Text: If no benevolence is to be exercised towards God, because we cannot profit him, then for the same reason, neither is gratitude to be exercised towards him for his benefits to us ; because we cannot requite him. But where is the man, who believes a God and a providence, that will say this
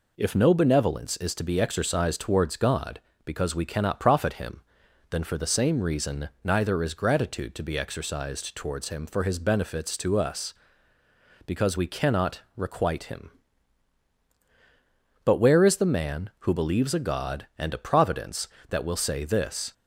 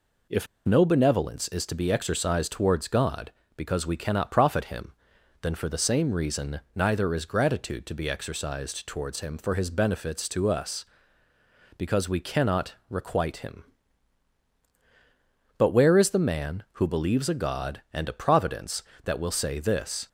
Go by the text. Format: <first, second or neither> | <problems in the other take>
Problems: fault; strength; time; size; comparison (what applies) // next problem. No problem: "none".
first | pauses between "If" and "no"; slight; at 0.4 s; 0.19 s long